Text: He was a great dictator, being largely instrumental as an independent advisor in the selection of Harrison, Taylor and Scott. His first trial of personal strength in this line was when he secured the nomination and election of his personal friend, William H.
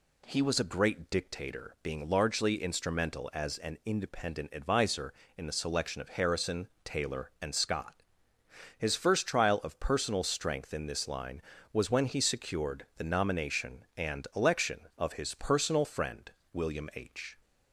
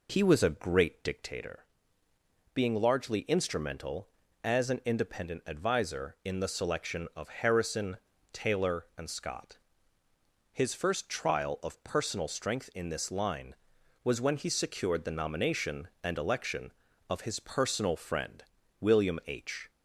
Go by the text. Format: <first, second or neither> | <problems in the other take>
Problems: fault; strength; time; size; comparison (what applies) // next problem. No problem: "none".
first | starts louder than the rest; until 1.4 s; 3.5 dB